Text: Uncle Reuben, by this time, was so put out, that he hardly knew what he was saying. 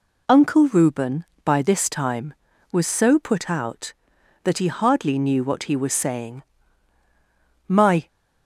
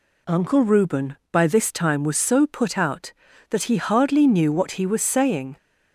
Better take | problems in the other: second | goes on to say "My"; slight; from 7.6 s on; 0.40 s long

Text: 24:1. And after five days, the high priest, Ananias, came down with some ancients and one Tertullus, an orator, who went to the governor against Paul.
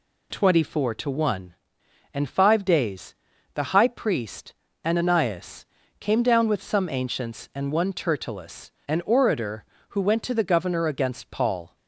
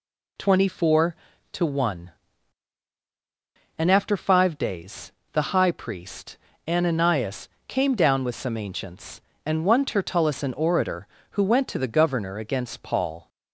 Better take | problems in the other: second | skips "after"; at 2.2 s

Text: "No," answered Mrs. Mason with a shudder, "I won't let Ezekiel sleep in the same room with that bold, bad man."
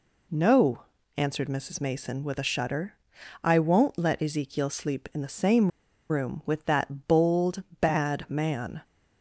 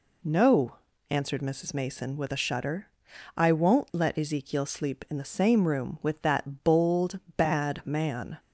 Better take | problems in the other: second | pauses between "same" and "room"; at 5.7 s; 0.39 s long

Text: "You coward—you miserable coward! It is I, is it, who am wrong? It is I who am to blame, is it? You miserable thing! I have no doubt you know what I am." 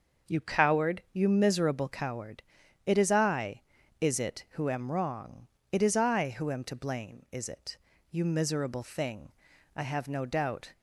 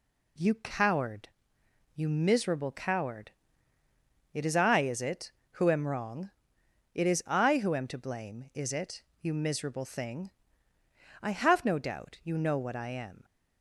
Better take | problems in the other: second | starts louder than the rest; until 1.3 s; 6.5 dB // stops before "you know what I am"; at 10.7 s

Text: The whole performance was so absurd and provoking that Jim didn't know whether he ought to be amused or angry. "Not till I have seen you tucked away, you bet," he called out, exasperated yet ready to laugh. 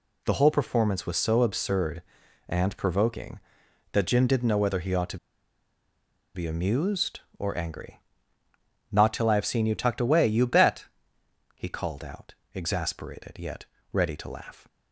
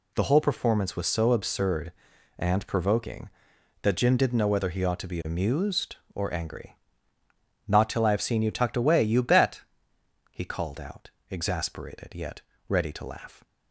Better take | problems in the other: second | pauses between "to" and "be"; at 5.1 s; 1.1 s long // pauses between "yet" and "ready"; slight; at 13.6 s; 0.30 s long; slight in the second

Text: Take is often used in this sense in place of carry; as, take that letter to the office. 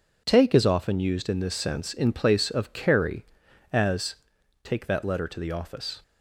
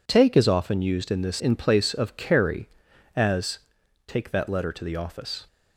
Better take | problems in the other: first | skips "sense"; at 1.3 s

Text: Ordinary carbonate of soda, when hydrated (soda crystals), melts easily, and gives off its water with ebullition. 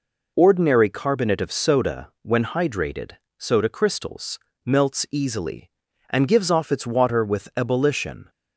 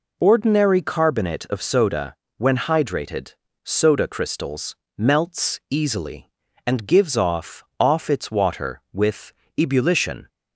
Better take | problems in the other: first | says "off" twice; at 7.7 s // pauses between "with" and "ebullition"; slight; at 9.3 s; 0.24 s long

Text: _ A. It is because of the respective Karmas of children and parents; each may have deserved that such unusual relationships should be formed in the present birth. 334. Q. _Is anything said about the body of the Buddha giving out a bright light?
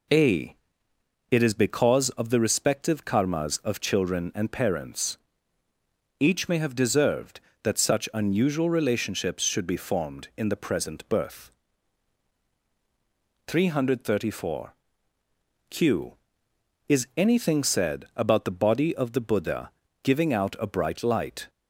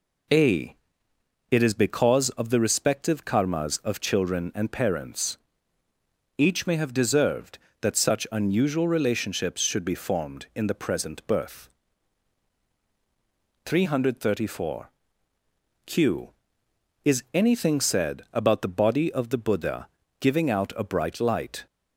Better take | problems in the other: neither | pauses between "Buddha" and "giving"; slight; the same in both

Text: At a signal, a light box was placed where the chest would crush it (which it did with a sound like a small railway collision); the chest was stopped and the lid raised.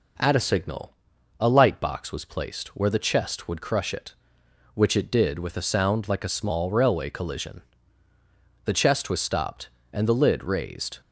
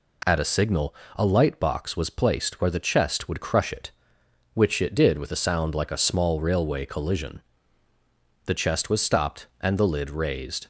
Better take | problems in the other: neither | none

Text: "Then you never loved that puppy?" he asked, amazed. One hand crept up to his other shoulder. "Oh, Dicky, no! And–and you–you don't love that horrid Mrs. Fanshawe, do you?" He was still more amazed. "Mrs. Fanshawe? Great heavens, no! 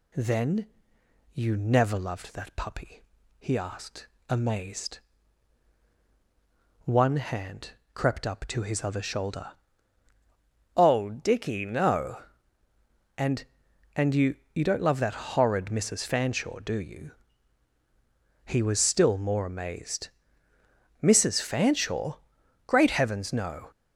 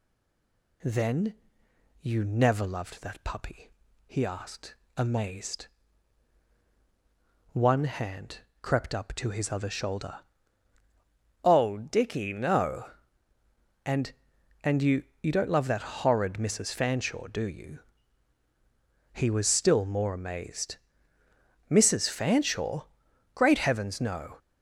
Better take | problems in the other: first | stays silent before the first word; slight; until 0.8 s; 0.8 s long // pauses between "Then" and "you"; noticeable; at 1.3 s; 0.68 s long; noticeable in the first // pauses between "hand" and "crept"; slight; at 8.3 s; 0.24 s long; slight in the first

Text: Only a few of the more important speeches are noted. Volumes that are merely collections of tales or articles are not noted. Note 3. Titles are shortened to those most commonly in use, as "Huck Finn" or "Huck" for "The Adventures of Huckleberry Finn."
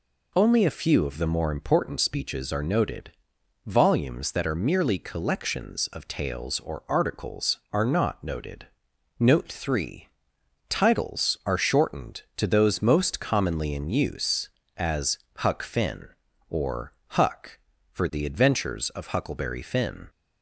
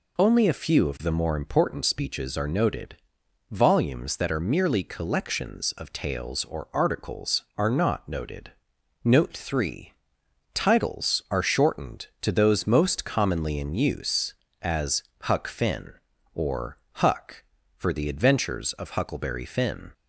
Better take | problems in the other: neither | pauses between "as" and "Huck"; slight; the same in both // pauses between "or" and "Huck"; slight; the same in both

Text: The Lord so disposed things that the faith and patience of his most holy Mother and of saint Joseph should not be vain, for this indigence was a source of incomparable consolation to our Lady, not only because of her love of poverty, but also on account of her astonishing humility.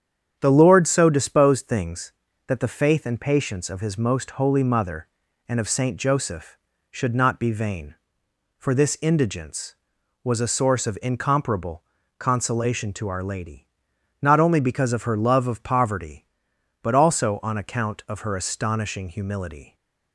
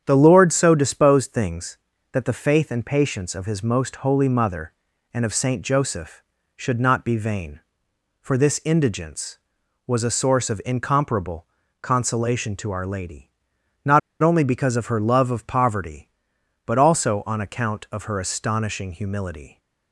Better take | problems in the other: first | starts louder than the rest; strong; until 1.0 s; 8.5 dB; strong in the first // pauses between "incomparable" and "consolation"; slight; at 11.4 s; 0.36 s long; slight in the first // pauses between "not" and "only"; slight; at 13.9 s; 0.23 s long

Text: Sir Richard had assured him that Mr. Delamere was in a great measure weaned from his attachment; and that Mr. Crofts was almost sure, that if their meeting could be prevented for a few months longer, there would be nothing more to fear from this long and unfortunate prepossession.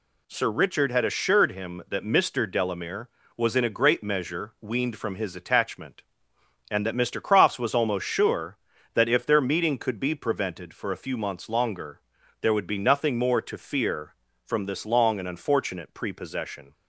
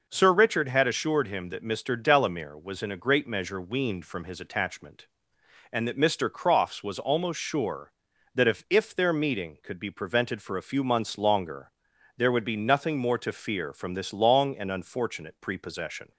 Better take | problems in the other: first | says "if" twice; at 8.6 s

